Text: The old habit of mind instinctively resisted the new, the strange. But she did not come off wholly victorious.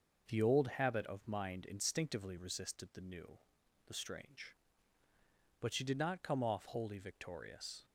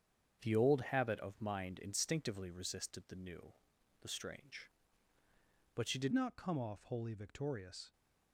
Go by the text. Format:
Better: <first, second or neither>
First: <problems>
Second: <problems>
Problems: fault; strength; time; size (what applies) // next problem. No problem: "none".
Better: first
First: none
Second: starts louder than the rest; strong; until 1.4 s; 7.5 dB // changes voice at "not"; from 6.1 s on; 1.8 s long